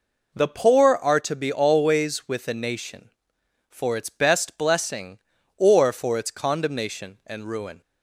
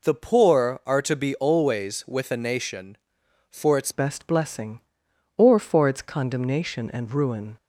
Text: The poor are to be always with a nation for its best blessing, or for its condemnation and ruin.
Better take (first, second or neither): first